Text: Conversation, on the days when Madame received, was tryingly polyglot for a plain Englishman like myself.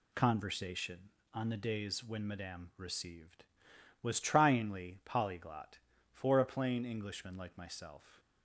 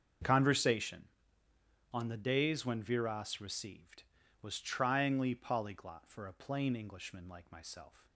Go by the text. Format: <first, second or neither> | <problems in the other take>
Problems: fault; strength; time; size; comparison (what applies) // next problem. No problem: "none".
first | starts louder than the rest; until 2.0 s; 7 dB // says "Viras" for "Madame"; at 2.8 s